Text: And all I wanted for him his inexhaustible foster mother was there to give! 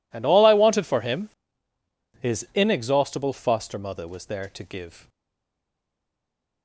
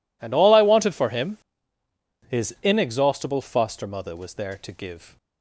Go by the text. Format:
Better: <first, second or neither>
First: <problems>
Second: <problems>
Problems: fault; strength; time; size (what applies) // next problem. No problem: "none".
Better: second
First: pauses between "him" and "his"; noticeable; at 1.2 s; 0.92 s long // stays silent after the last word; noticeable; from 5.0 s on; 1.6 s long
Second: pauses between "him" and "his"; noticeable; at 1.3 s; 0.92 s long